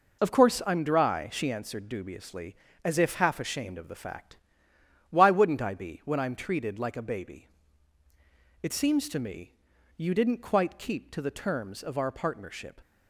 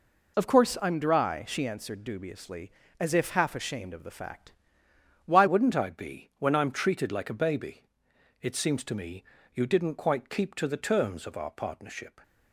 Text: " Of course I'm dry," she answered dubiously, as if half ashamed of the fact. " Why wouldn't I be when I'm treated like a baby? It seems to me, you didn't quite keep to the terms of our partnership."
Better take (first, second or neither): first